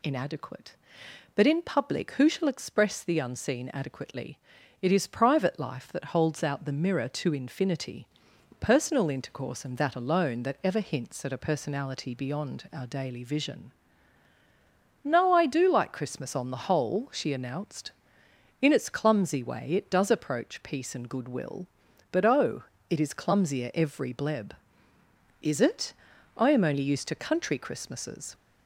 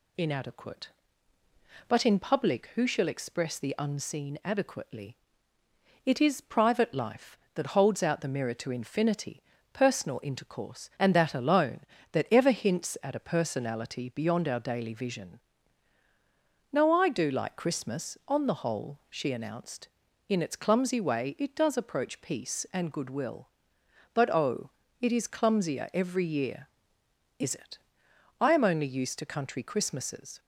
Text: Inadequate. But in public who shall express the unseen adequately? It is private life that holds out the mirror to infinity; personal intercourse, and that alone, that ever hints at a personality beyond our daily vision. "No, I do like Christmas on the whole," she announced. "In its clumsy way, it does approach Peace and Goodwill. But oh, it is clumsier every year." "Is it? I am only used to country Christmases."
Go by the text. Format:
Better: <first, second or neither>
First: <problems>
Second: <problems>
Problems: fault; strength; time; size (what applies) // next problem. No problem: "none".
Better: second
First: says "bleb" for "year"; at 24.1 s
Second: none